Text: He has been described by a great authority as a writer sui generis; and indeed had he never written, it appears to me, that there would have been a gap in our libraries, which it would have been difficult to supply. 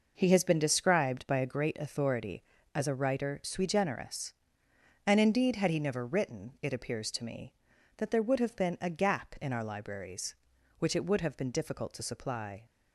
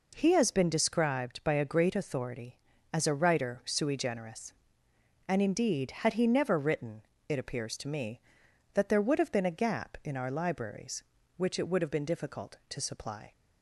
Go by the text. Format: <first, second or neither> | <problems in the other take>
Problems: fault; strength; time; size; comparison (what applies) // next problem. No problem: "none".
neither | none